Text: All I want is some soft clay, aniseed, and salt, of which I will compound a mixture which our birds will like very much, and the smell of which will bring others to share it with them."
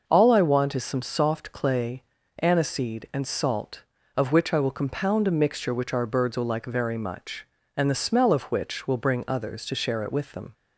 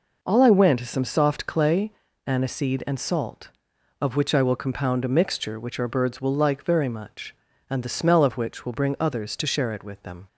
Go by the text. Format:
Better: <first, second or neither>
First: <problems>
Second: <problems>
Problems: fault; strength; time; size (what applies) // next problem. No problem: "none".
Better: first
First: none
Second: says "went" for "want"; at 0.5 s